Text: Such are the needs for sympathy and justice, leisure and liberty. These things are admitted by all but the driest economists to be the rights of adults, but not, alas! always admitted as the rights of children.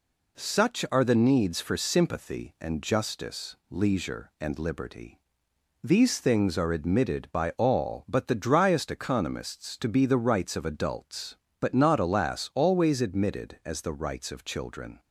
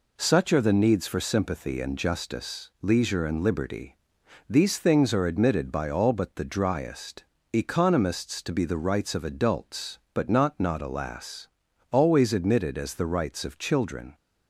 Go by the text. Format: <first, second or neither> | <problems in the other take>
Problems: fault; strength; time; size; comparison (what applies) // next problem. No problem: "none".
first | pauses between "driest" and "economists"; slight; at 7.2 s; 0.29 s long // says "not" twice; at 10.5 s